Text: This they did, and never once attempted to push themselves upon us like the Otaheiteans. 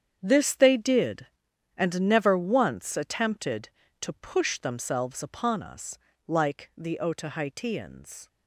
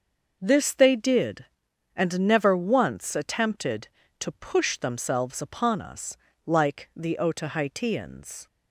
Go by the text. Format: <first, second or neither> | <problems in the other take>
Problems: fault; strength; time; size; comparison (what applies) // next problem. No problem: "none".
second | gets quieter; strong; throughout; 13.5 dB // starts louder than the rest; strong; until 1.2 s; 8 dB; noticeable in the second // pauses between "us" and "like"; slight; at 5.9 s; 0.26 s long; slight in the second